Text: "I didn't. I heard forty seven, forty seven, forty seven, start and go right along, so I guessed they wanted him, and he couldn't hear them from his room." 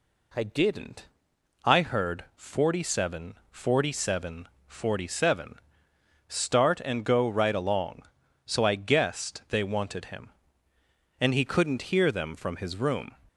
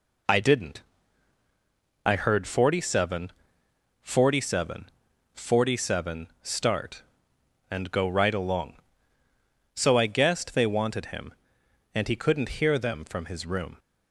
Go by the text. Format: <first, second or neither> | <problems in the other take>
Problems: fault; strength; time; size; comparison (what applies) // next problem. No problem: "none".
neither | none